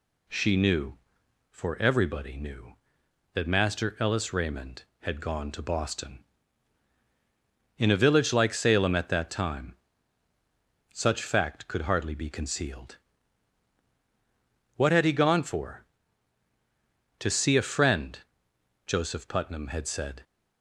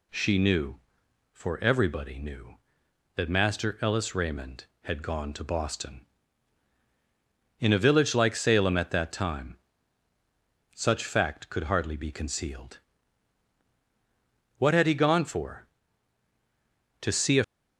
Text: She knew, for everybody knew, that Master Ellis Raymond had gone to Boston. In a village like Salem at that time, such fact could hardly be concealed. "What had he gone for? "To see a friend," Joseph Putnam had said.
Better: first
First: none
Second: stops before "friend Joseph Putnam had said"; at 17.4 s

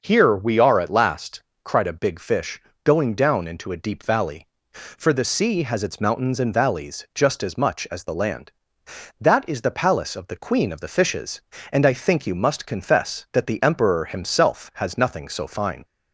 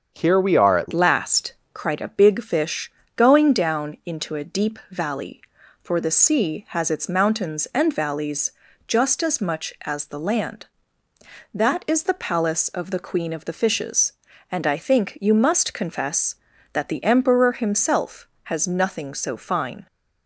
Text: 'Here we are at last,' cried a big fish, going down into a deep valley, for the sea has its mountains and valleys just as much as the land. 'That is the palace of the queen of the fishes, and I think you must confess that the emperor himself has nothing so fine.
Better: first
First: starts louder than the rest; until 1.0 s; 6.5 dB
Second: starts louder than the rest; until 1.1 s; 7 dB // changes voice at "last"; from 0.9 s on; 18.9 s long // pauses between "valleys" and "just"; slight; at 8.5 s; 0.36 s long

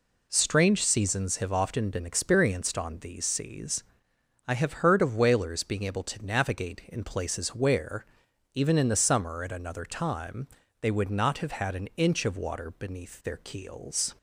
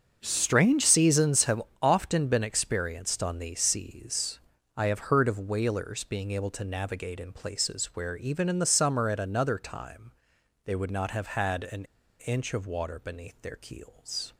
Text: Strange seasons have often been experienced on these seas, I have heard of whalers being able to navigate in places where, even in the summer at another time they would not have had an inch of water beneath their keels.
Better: first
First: pauses between "time" and "they"; slight; at 10.4 s; 0.34 s long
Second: starts louder than the rest; until 1.2 s; 6.5 dB // pauses between "have" and "often"; slight; at 1.6 s; 0.18 s long // pauses between "time" and "they"; noticeable; at 10.1 s; 0.54 s long // pauses between "an" and "inch"; slight; at 11.8 s; 0.34 s long

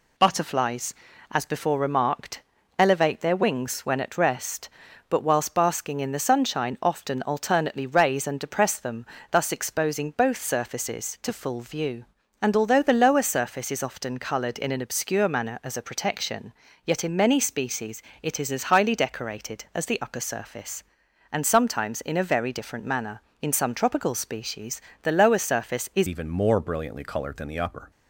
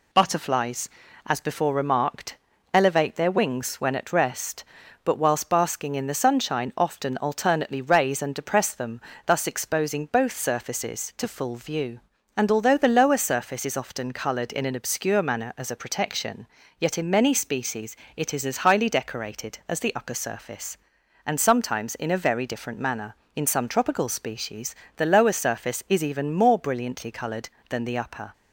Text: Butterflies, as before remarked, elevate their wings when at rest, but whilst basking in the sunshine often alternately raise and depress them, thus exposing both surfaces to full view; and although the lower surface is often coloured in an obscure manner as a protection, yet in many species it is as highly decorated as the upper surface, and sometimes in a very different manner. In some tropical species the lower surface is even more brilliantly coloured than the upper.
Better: second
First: pauses between "species" and "it"; slight; at 18.0 s; 0.22 s long // pauses between "species" and "the"; slight; at 24.8 s; 0.22 s long // changes voice at "even"; from 26.0 s on; 1.9 s long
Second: pauses between "species" and "it"; slight; at 17.9 s; 0.22 s long // pauses between "species" and "the"; slight; at 24.7 s; 0.22 s long

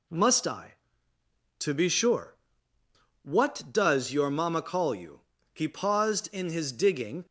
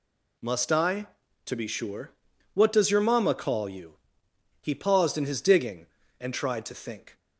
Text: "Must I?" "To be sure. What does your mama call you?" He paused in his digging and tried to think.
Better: second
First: stops before "and tried to think"; at 7.2 s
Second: none

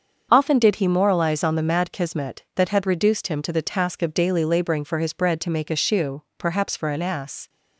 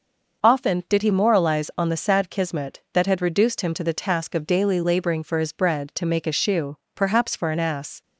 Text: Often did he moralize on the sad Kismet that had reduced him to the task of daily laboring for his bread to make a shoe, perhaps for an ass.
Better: second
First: starts louder than the rest; until 1.3 s; 7 dB // says "mad" for "sad"; at 1.6 s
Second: none

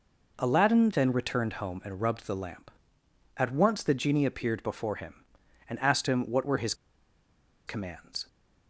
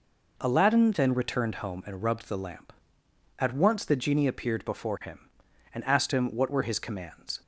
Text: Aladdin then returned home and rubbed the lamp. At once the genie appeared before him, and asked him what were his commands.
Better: second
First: pauses between "his" and "commands"; noticeable; at 6.7 s; 0.92 s long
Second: none

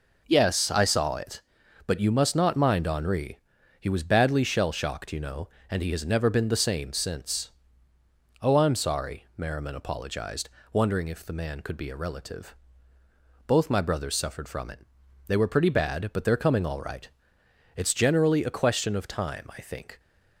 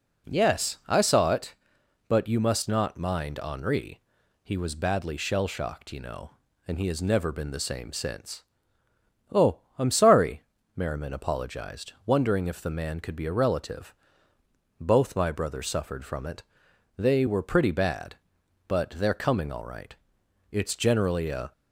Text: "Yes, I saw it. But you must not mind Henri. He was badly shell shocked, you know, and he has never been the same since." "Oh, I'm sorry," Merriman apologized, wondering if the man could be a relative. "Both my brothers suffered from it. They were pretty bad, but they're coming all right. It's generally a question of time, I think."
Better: first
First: none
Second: stops before "question of time I think"; at 21.5 s

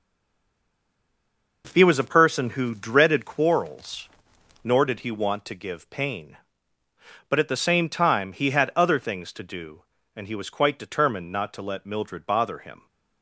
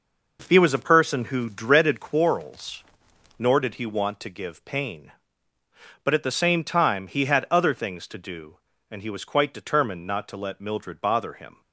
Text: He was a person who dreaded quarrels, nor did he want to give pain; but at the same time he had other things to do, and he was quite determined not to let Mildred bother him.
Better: second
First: stays silent before the first word; noticeable; until 1.6 s; 1.6 s long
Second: none

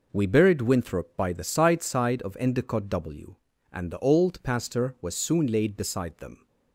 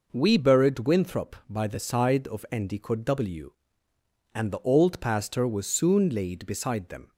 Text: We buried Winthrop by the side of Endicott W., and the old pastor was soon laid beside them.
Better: second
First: says "side" twice; at 1.8 s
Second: none

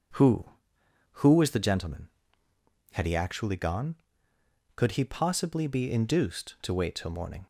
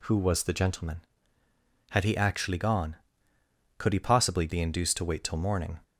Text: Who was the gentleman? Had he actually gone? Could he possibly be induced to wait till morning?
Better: second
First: says "Who" twice; at 1.1 s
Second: none

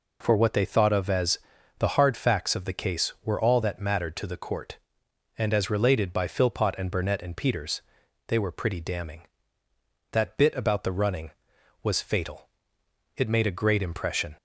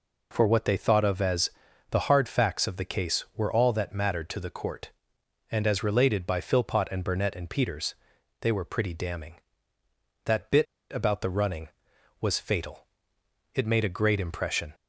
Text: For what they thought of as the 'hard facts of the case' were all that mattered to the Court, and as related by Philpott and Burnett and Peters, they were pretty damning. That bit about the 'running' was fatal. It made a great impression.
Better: first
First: pauses between "as" and "the"; at 1.3 s; 0.40 s long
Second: pauses between "as" and "the"; at 1.4 s; 0.40 s long // pauses between "bit" and "about"; slight; at 10.6 s; 0.26 s long

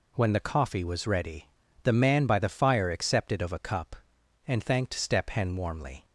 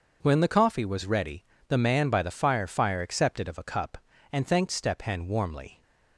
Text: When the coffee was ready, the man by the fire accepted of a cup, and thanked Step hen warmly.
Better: first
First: none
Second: starts louder than the rest; noticeable; until 1.2 s; 6 dB // says "fire" twice; at 2.6 s

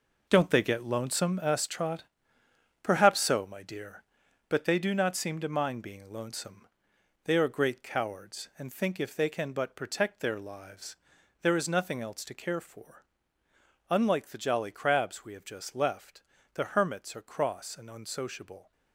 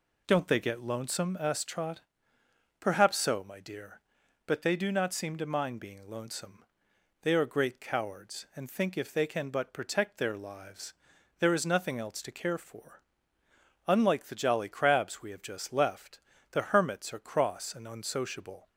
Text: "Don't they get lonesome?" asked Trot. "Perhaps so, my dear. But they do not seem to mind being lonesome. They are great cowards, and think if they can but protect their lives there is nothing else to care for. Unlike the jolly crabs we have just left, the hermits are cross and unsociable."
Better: second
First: gets quieter; strong; throughout; 9 dB // pauses between "lives" and "there"; noticeable; at 10.9 s; 0.46 s long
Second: pauses between "lives" and "there"; noticeable; at 10.9 s; 0.46 s long

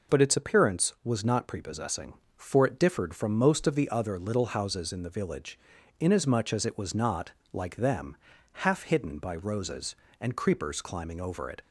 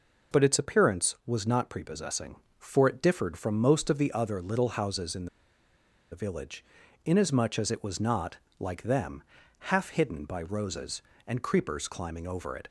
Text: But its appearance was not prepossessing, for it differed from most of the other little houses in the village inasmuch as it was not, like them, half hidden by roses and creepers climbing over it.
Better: first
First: pauses between "village" and "inasmuch"; at 5.5 s; 0.42 s long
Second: pauses between "in" and "the"; noticeable; at 5.2 s; 0.85 s long // pauses between "village" and "inasmuch"; at 6.6 s; 0.42 s long

